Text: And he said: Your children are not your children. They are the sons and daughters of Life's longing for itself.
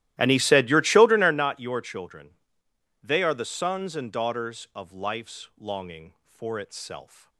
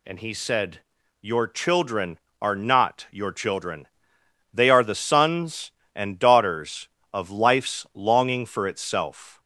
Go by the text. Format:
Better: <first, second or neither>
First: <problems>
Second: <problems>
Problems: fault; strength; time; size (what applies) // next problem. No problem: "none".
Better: second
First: starts louder than the rest; strong; until 1.4 s; 14.5 dB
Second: none